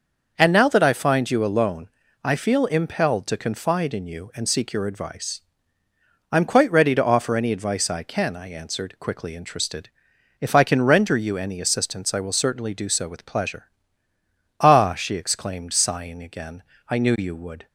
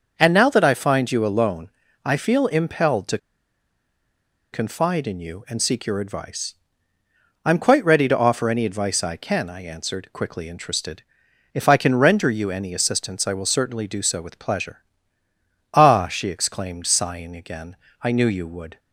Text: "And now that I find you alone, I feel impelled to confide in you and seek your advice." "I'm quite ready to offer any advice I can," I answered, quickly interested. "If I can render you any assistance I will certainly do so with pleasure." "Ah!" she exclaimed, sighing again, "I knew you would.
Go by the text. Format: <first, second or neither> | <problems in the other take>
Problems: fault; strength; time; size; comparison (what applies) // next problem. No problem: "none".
first | starts louder than the rest; until 1.2 s; 6 dB; also in the first // pauses between "to" and "confide"; strong; at 3.1 s; 1.3 s long